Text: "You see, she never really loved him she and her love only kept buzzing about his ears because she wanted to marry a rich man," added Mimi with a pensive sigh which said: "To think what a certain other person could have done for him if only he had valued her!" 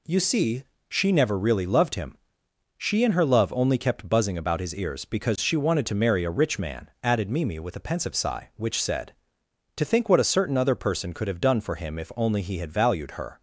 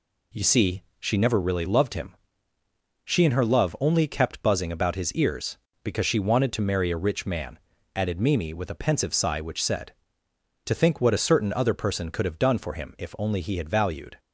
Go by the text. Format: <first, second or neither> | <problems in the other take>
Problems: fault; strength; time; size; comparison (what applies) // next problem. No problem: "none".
first | pauses between "him" and "she"; noticeable; at 2.1 s; 0.90 s long; noticeable in the first // stops before "her"; at 14.1 s